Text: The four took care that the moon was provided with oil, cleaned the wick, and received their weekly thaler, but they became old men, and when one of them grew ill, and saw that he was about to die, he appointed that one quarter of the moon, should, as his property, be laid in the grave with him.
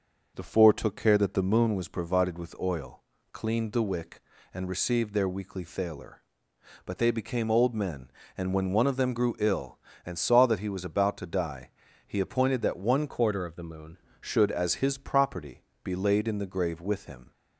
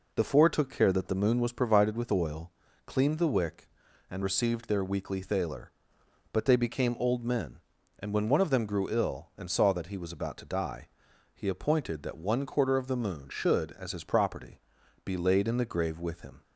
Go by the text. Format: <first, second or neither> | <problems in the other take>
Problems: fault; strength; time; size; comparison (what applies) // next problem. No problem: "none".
second | changes voice from "quarter" to "moon"; from 13.0 to 13.9 s; 0.9 s long